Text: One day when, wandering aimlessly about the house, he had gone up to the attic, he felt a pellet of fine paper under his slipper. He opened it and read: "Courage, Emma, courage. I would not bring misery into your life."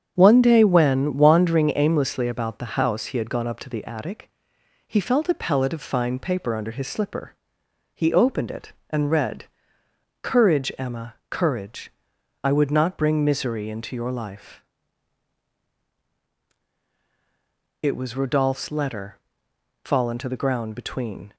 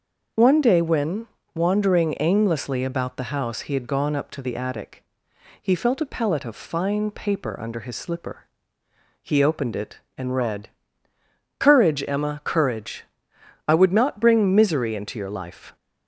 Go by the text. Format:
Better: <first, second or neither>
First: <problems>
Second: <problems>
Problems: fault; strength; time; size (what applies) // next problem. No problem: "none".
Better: second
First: starts louder than the rest; strong; until 1.1 s; 8 dB // goes on to say "It was Rodolphe's letter fallen to the ground between"; strong; from 17.8 s on; 3.5 s long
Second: starts louder than the rest; noticeable; until 1.6 s; 6 dB